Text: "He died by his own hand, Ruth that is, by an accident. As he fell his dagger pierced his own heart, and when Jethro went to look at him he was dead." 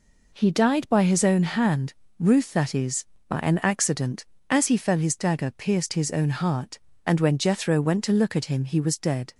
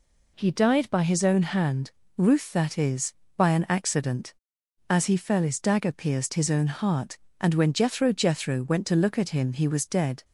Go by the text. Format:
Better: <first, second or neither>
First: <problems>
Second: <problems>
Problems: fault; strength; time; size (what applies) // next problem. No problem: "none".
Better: first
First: none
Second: says "Jethro" twice; at 8.1 s